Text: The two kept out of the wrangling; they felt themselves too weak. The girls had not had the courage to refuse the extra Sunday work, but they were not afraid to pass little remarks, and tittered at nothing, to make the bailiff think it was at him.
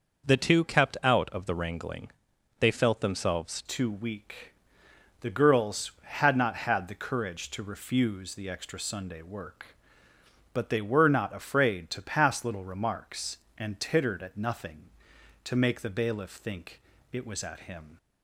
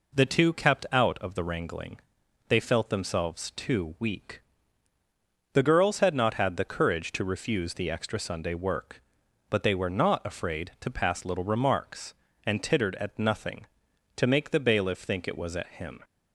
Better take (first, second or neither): second